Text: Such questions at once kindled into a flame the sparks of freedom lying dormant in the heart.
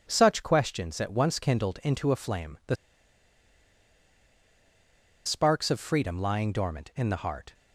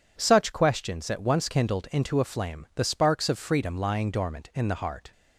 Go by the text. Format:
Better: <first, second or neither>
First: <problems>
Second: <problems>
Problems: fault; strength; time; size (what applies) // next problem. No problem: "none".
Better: second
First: pauses between "the" and "sparks"; strong; at 2.7 s; 2.5 s long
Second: none